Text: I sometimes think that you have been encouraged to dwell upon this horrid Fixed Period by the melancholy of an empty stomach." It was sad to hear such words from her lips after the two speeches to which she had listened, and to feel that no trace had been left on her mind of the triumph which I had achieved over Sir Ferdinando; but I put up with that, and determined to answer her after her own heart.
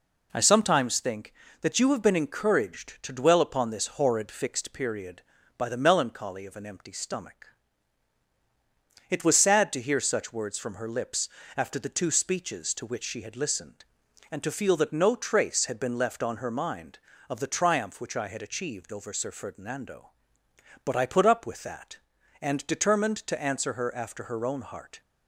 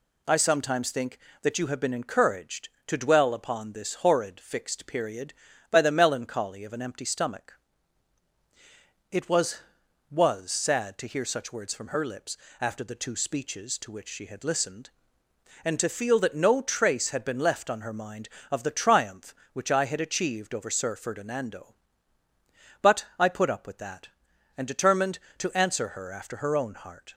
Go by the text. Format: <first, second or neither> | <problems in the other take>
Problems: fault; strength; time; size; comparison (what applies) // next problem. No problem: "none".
first | says "was" twice; at 10.1 s // pauses between "lips" and "after"; slight; at 12.3 s; 0.24 s long; slight in the first